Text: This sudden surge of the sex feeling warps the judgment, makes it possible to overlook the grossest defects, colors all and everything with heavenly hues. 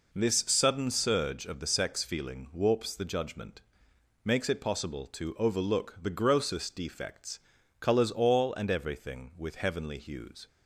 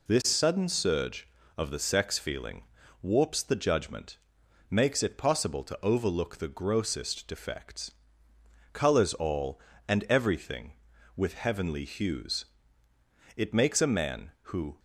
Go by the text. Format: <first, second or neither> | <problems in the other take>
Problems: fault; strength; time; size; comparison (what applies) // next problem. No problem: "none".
first | pauses between "feeling" and "warps"; at 2.6 s; 0.40 s long // goes on to say "It makes a man who"; from 13.3 s on; 1.4 s long